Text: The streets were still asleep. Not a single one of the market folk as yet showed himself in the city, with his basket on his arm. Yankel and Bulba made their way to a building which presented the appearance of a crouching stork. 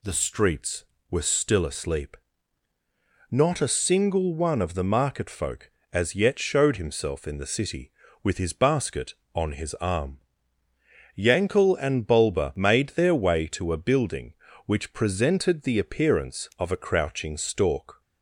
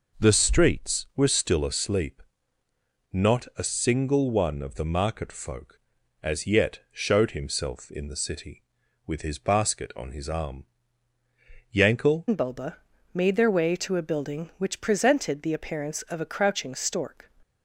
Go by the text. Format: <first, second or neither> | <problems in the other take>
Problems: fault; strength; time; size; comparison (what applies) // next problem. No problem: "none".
first | changes voice at "and"; from 12.2 s on; 5.0 s long // pauses between "Bulba" and "made"; slight; at 12.7 s; 0.36 s long